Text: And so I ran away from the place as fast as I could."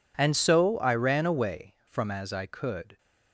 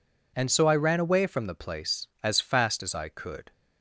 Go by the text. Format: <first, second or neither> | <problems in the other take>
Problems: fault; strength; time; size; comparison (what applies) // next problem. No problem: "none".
second | skips "the place as fast"; at 2.0 s